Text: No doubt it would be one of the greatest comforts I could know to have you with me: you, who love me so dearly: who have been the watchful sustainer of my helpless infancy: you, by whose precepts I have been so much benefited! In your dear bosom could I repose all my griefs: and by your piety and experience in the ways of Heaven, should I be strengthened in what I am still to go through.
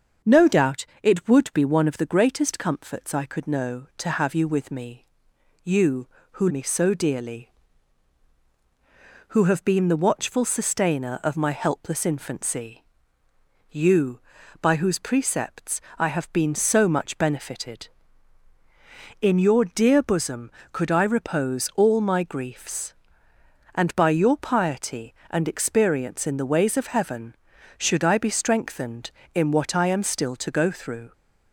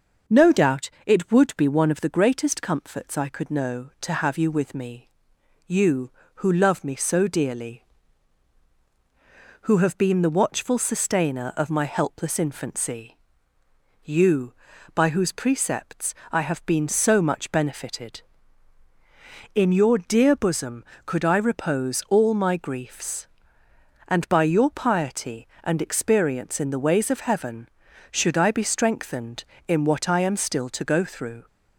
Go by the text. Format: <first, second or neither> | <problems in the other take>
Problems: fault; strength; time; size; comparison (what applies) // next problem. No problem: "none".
second | starts louder than the rest; until 1.4 s; 6.5 dB; noticeable in the second // pauses between "doubt" and "it"; slight; at 0.8 s; 0.16 s long // skips "love"; at 6.4 s // pauses between "precepts" and "I"; slight; at 15.8 s; 0.16 s long; slight in the second